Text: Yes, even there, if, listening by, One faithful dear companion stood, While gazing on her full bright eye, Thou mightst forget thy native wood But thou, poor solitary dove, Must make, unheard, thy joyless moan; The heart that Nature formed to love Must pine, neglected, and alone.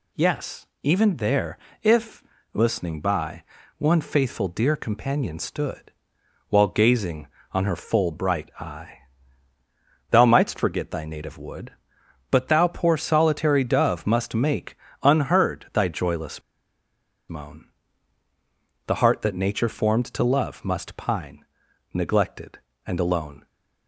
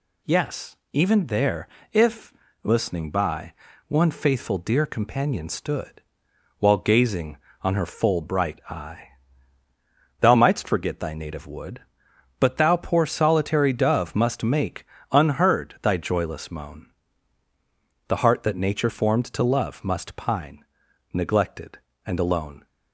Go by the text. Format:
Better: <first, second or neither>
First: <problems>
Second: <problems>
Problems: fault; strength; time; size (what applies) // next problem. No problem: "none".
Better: second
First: pauses between "joyless" and "moan"; noticeable; at 16.4 s; 0.88 s long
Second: none